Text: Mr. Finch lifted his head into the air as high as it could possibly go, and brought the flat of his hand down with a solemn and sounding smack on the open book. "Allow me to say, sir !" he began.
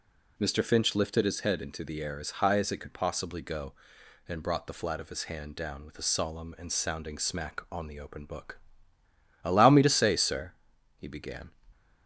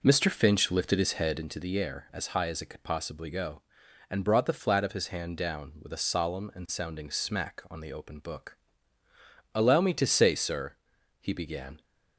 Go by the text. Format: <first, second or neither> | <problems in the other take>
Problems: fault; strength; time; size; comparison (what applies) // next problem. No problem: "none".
first | starts louder than the rest; noticeable; until 1.5 s; 4.5 dB